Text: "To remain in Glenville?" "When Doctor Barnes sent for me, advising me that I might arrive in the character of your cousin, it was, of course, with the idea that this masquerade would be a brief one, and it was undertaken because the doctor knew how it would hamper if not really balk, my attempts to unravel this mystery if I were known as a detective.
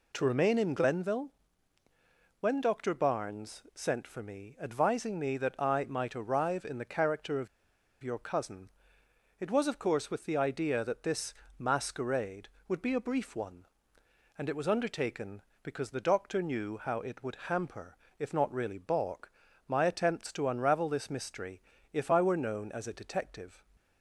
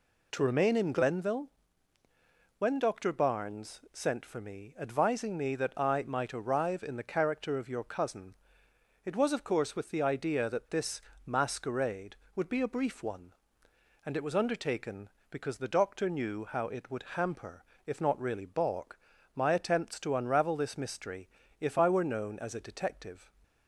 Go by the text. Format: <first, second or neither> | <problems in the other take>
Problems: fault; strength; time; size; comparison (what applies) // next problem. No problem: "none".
second | pauses between "of" and "your"; noticeable; at 7.4 s; 0.55 s long // pauses between "this" and "masquerade"; slight; at 11.3 s; 0.26 s long; slight in the second // pauses between "hamper" and "if"; slight; at 17.9 s; 0.20 s long; slight in the second // pauses between "mystery" and "if"; slight; at 21.6 s; 0.30 s long; slight in the second